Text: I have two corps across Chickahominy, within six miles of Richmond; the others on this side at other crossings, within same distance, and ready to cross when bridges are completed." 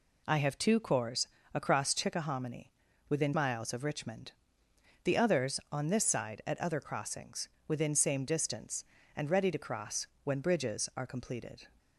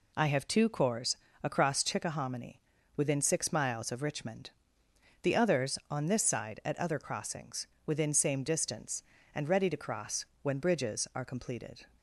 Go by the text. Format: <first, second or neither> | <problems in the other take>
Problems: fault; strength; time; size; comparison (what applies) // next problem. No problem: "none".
second | pauses between "corps" and "across"; slight; at 1.2 s; 0.26 s long; slight in the second // skips "six"; at 3.3 s // pauses between "cross" and "when"; slight; at 10.0 s; 0.16 s long; slight in the second